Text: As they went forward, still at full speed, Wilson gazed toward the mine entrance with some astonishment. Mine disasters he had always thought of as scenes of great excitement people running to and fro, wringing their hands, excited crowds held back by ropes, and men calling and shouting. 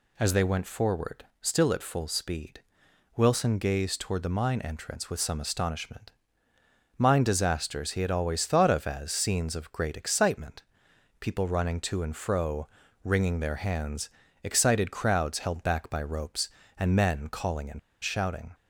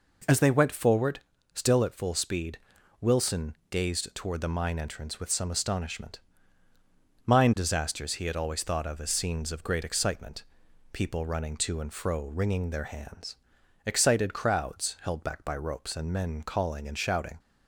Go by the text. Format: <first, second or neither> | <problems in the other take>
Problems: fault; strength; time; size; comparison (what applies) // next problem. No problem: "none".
second | pauses between "excitement" and "people"; noticeable; at 10.6 s; 0.56 s long; noticeable in the second // pauses between "and" and "shouting"; slight; at 17.7 s; 0.22 s long